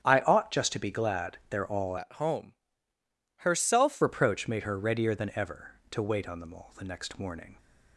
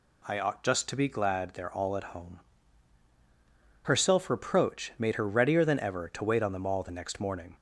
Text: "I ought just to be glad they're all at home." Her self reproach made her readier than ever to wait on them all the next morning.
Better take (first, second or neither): second